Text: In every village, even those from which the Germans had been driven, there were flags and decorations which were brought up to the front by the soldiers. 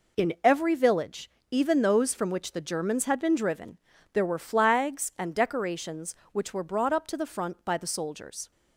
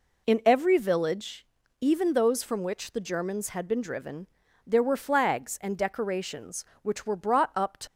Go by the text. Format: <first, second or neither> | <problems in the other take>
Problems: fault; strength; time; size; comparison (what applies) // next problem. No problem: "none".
first | stops before "the front by the soldiers"; at 7.8 s